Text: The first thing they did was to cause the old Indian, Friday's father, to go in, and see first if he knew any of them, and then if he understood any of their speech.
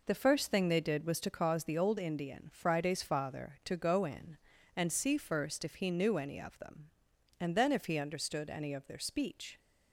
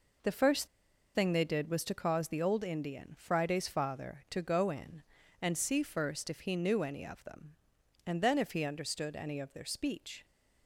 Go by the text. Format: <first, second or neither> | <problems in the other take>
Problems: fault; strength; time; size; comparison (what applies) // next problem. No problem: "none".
first | pauses between "first" and "thing"; noticeable; at 0.6 s; 0.47 s long